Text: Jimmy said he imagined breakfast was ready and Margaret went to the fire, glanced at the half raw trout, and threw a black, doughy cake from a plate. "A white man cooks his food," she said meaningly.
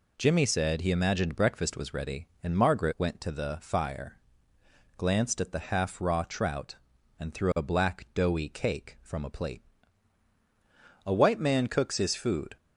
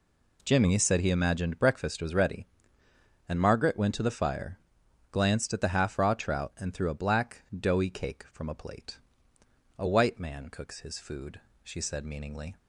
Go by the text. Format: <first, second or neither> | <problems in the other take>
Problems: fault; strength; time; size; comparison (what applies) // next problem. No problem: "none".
second | stops before "she said meaningly"; at 12.5 s